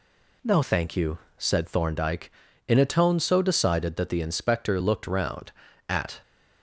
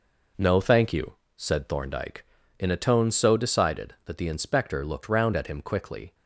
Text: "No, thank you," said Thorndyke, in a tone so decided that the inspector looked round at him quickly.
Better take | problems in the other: second | stops before "him quickly"; at 6.2 s

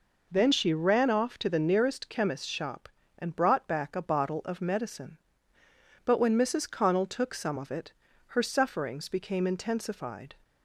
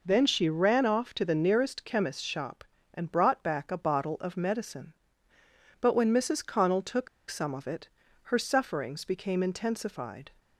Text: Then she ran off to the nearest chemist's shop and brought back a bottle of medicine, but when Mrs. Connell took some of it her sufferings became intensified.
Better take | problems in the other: first | pauses between "took" and "some"; slight; at 7.0 s; 0.21 s long // pauses between "it" and "her"; slight; at 7.8 s; 0.36 s long; slight in the first

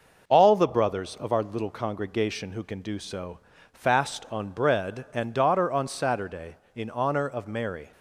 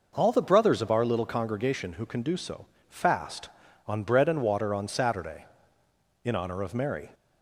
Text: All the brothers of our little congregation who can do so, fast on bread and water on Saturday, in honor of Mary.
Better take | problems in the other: second | says "daughter" for "water"; at 5.3 s

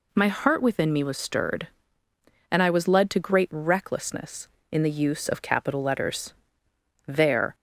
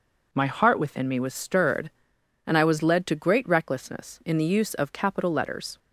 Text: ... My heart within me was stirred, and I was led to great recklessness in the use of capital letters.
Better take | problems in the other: second | goes on to say "There"; slight; from 7.0 s on; 0.48 s long

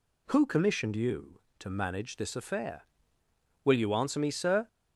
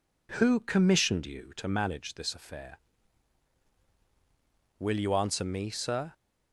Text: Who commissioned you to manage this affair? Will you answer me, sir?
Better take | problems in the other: neither | none

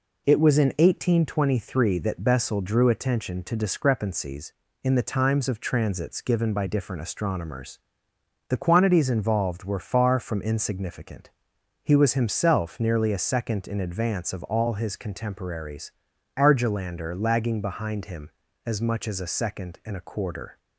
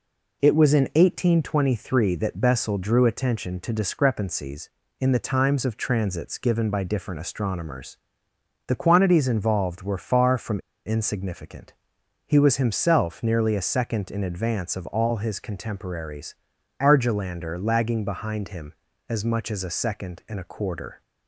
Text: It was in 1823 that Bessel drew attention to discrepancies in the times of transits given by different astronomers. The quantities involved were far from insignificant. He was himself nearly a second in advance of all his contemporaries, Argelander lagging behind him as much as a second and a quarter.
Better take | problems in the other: first | pauses between "from" and "insignificant"; slight; at 10.5 s; 0.28 s long

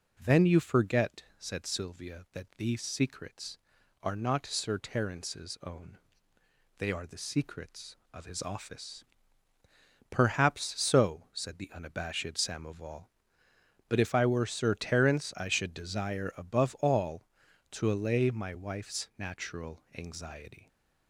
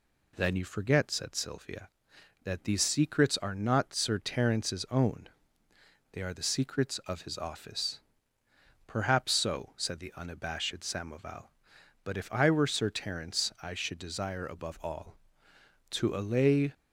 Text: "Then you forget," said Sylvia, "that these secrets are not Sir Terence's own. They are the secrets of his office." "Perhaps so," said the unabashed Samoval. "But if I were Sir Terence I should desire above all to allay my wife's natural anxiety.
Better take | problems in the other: first | stops before "my wife's natural anxiety"; at 16.7 s

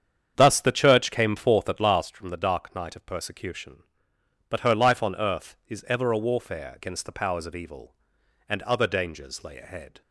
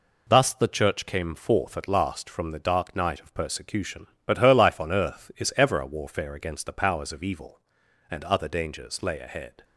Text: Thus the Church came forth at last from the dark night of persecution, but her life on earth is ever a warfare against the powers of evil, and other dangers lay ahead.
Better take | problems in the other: second | starts louder than the rest; strong; until 2.1 s; 8 dB

